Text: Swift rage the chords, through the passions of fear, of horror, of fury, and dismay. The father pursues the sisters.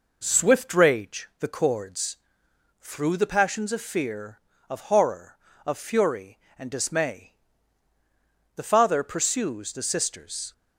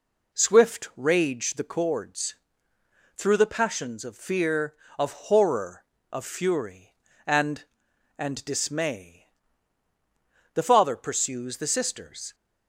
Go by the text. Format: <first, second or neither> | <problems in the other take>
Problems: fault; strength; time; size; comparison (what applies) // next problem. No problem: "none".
first | says "and" twice; at 8.1 s